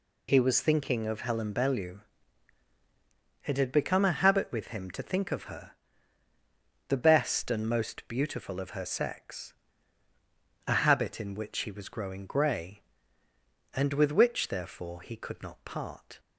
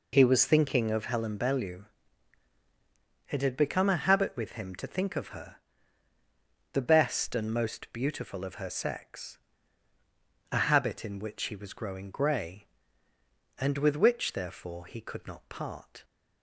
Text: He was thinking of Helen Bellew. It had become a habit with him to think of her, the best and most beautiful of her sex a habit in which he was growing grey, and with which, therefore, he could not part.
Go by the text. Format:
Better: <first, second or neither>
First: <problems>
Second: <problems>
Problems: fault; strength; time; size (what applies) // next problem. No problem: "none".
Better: first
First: pauses between "sex" and "a"; at 9.5 s; 1.1 s long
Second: starts louder than the rest; until 1.2 s; 4 dB // pauses between "sex" and "a"; at 9.3 s; 1.1 s long